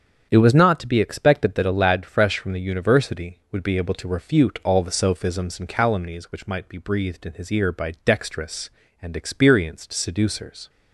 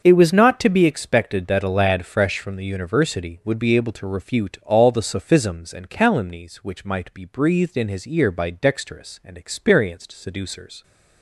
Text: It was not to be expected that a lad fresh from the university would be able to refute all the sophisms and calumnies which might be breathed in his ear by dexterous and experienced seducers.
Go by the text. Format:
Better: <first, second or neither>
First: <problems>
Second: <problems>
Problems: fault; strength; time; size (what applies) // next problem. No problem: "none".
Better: neither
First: starts louder than the rest; strong; until 1.3 s; 8 dB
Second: starts louder than the rest; until 1.0 s; 7 dB